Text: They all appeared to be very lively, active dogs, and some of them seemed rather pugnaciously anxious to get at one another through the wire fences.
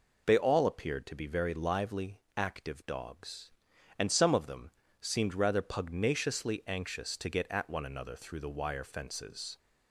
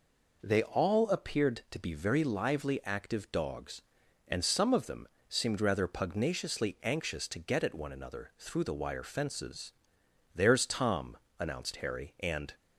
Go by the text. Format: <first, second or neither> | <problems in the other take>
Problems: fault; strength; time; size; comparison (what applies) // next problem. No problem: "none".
first | pauses between "them" and "seemed"; slight; at 5.0 s; 0.22 s long; slight in the first // goes on to say "There's Tom announced Harry and"; strong; from 10.3 s on; 2.2 s long